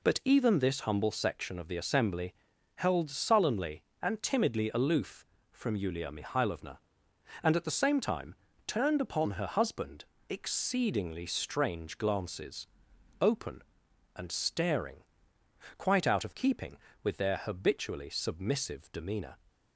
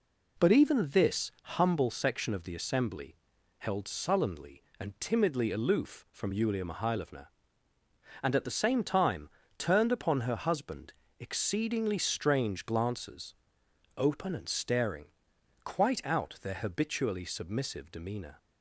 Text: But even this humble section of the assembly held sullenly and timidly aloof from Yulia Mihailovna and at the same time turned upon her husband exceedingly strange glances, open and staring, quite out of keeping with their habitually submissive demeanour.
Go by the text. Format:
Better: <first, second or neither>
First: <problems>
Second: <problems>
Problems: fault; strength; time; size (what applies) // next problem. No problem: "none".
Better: first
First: pauses between "assembly" and "held"; at 2.3 s; 0.42 s long // pauses between "time" and "turned"; slight; at 8.3 s; 0.32 s long // pauses between "husband" and "exceedingly"; slight; at 10.0 s; 0.24 s long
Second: pauses between "assembly" and "held"; at 3.1 s; 0.42 s long // pauses between "time" and "turned"; slight; at 9.2 s; 0.28 s long // pauses between "husband" and "exceedingly"; slight; at 10.9 s; 0.26 s long // skips "of keeping with"; at 16.3 s